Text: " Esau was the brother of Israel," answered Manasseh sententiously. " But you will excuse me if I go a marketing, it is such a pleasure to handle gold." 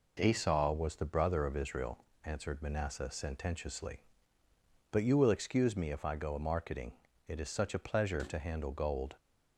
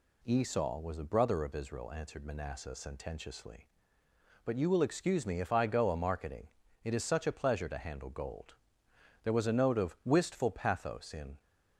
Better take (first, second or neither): first